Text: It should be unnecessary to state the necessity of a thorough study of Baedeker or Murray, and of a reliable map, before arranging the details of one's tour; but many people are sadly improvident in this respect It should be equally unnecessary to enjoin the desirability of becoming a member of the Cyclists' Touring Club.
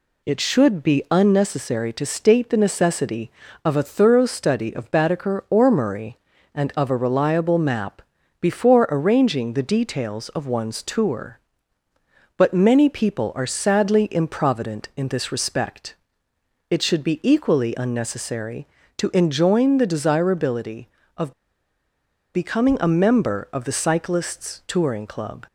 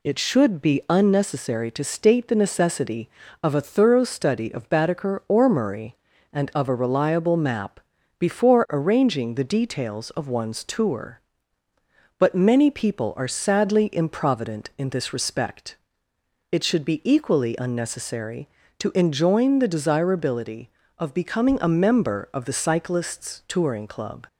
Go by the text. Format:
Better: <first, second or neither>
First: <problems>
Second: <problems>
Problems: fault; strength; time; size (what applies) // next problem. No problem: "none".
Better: second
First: pauses between "respect" and "It"; noticeable; at 15.9 s; 0.74 s long // pauses between "of" and "becoming"; at 21.3 s; 1.0 s long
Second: pauses between "respect" and "It"; noticeable; at 15.7 s; 0.74 s long